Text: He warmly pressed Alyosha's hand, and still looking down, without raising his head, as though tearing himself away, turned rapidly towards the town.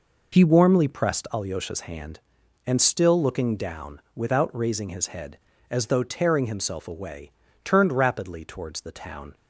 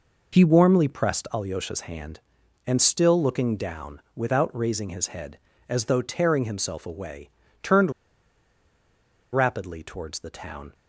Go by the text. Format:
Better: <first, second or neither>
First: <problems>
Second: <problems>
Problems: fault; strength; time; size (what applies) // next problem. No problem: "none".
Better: first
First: none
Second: pauses between "turned" and "rapidly"; strong; at 7.9 s; 1.4 s long